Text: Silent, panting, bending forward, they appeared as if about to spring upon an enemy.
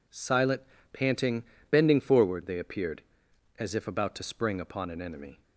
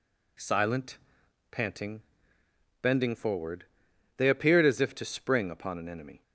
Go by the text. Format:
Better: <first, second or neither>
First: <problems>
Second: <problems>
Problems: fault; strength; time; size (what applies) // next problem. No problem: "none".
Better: first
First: none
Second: skips "about"; at 4.9 s